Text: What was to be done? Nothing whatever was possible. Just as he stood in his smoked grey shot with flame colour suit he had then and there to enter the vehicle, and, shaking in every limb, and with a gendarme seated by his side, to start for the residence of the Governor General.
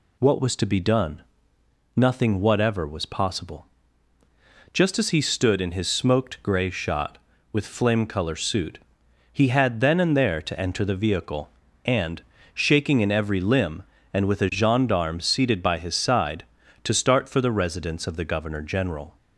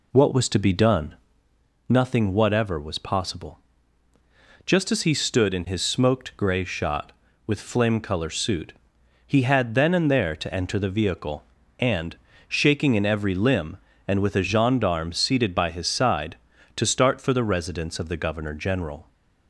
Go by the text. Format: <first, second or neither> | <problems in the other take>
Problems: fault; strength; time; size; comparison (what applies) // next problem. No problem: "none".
first | starts louder than the rest; slight; until 1.4 s; 2.5 dB // pauses between "suit" and "he"; noticeable; at 8.7 s; 0.54 s long; noticeable in the first